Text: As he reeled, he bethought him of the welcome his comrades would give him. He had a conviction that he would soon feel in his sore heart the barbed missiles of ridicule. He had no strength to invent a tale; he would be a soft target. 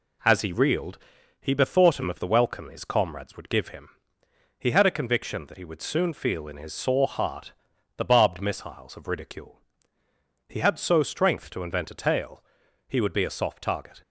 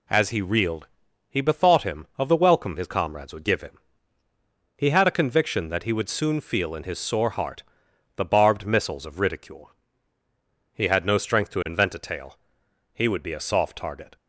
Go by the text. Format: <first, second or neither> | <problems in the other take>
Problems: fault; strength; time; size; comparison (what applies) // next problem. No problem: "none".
second | pauses between "heart" and "the"; at 7.5 s; 0.44 s long; noticeable in the second // says "so" for "no"; at 10.7 s